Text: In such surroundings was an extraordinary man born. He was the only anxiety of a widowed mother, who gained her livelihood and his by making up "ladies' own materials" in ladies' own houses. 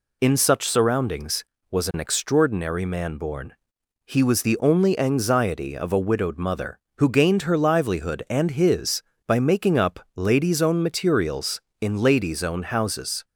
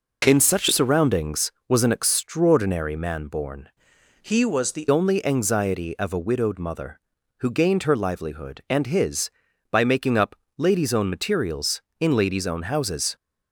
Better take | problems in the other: first | changes voice from "He" to "the"; from 4.2 to 4.8 s; 0.6 s long // pauses between "up" and "ladies"; slight; at 10.3 s; 0.22 s long; slight in the first

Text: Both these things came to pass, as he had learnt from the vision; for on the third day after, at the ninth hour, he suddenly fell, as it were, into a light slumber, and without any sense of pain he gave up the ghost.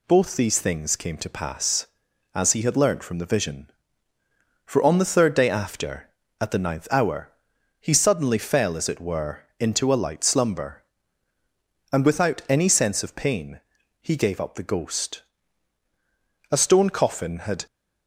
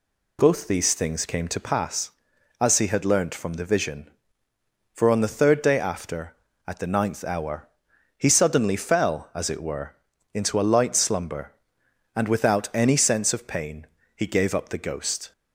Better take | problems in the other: second | pauses between "pain" and "he"; at 13.5 s; 0.42 s long; slight in the second // goes on to say "A stone coffin had"; noticeable; from 16.5 s on; 1.1 s long

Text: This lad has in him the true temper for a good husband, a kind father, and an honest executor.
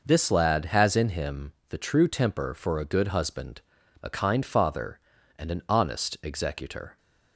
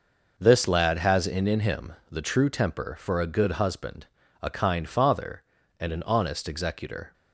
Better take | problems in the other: first | says "in" twice; at 1.4 s // pauses between "him" and "the"; slight; at 1.9 s; 0.18 s long; slight in the first

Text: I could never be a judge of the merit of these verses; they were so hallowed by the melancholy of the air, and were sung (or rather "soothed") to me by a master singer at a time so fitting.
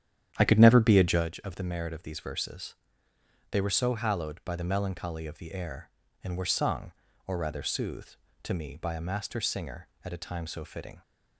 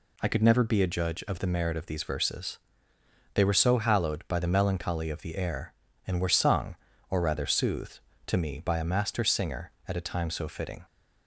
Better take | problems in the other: second | starts louder than the rest; strong; until 1.3 s; 10 dB

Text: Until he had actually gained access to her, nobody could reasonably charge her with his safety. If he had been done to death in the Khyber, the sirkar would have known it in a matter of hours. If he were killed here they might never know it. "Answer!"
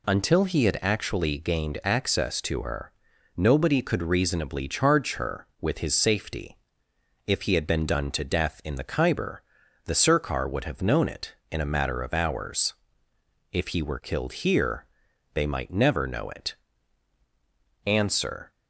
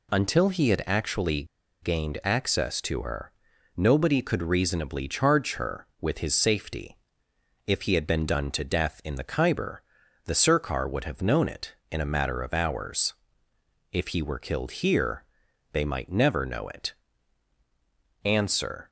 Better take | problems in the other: first | pauses between "actually" and "gained"; at 1.4 s; 0.38 s long // pauses between "here" and "they"; noticeable; at 15.2 s; 0.48 s long; noticeable in the first

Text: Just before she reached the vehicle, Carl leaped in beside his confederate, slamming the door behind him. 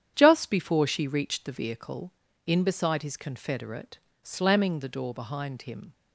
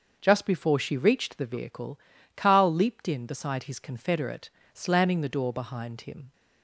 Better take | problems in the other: second | starts louder than the rest; strong; until 1.1 s; 9 dB; also in the second // skips "Carl leaped"; at 2.2 s

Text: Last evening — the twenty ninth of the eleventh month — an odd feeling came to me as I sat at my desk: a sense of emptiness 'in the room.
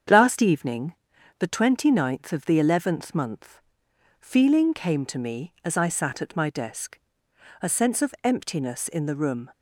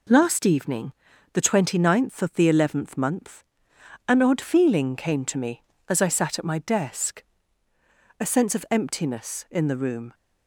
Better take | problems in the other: second | starts louder than the rest; strong; until 1.5 s; 8 dB // skips "an odd"; at 3.8 s

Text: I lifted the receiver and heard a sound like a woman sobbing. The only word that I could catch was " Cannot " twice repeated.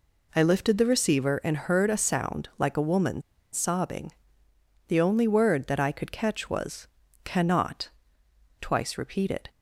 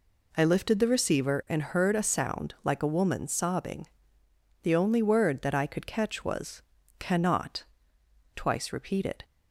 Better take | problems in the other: second | pauses between "woman" and "sobbing"; slight; at 3.2 s; 0.32 s long

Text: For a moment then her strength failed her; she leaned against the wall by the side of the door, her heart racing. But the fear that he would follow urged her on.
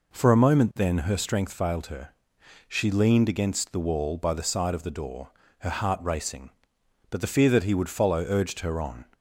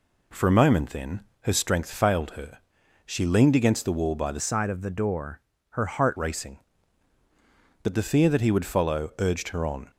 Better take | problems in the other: first | pauses between "then" and "her"; slight; at 1.1 s; 0.22 s long // changes voice from "side" to "heart"; from 4.3 to 6.1 s; 1.8 s long

